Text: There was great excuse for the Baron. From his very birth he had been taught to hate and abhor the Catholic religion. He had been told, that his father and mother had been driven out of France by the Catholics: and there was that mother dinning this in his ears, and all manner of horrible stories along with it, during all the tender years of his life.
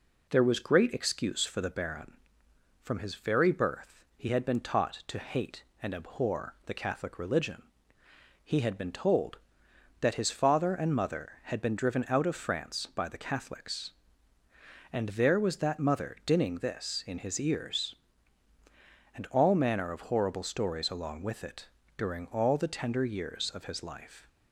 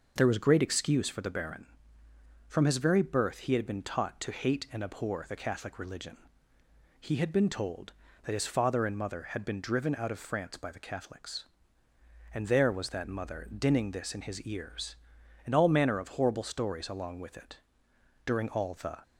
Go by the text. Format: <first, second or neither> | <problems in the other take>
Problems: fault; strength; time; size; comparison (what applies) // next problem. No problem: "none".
first | stops before "tender years of his life"; at 19.0 s